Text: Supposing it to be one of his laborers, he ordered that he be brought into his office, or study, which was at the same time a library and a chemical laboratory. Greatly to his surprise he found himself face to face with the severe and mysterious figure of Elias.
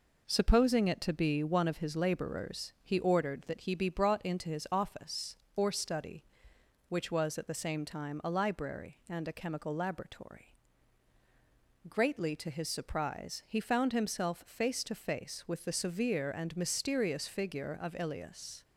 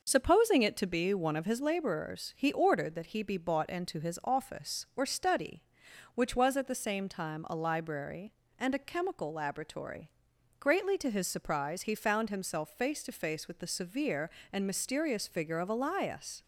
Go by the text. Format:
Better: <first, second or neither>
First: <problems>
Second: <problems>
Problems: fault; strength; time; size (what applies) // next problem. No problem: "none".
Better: first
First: none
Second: says "bought" for "brought"; at 3.3 s